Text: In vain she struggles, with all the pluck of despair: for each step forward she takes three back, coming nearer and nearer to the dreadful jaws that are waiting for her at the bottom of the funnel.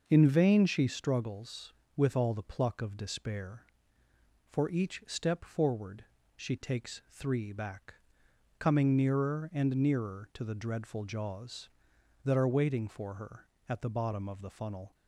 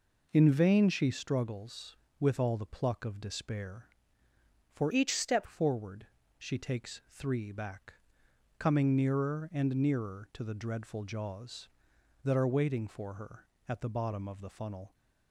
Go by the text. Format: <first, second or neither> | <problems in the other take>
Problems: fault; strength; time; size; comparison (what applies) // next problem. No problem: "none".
first | changes voice from "each" to "step"; from 4.9 to 5.4 s; 0.5 s long // pauses between "forward" and "she"; slight; at 6.0 s; 0.32 s long; slight in the first